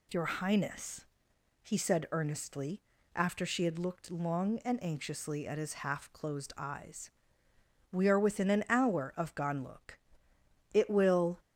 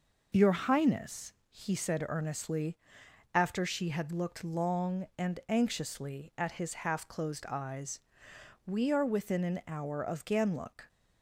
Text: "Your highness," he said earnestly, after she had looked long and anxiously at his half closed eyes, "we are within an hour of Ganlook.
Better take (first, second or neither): second